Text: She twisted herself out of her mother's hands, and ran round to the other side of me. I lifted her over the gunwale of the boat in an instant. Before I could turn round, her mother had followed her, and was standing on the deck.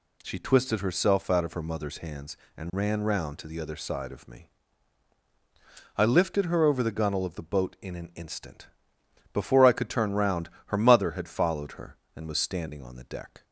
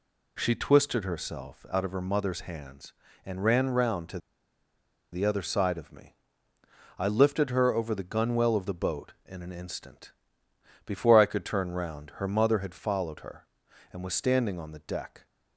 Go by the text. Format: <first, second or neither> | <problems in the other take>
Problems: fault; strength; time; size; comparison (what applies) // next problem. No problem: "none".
first | pauses between "to" and "the"; noticeable; at 4.1 s; 0.93 s long